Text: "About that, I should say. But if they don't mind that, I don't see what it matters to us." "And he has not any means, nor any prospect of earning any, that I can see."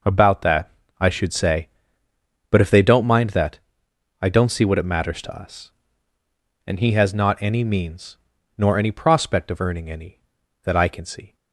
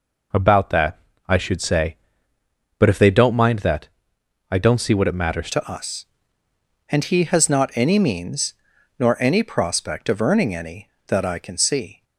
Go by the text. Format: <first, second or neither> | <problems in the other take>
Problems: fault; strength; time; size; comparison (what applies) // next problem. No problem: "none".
first | changes voice at "to"; from 5.5 s on; 6.5 s long